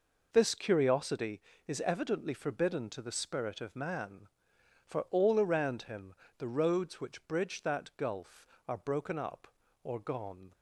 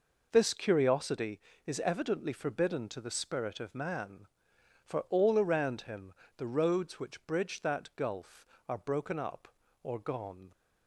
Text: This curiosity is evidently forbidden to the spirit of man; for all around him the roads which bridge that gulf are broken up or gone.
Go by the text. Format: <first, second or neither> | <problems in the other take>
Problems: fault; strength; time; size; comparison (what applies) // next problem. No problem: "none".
neither | pauses between "him" and "the"; slight; the same in both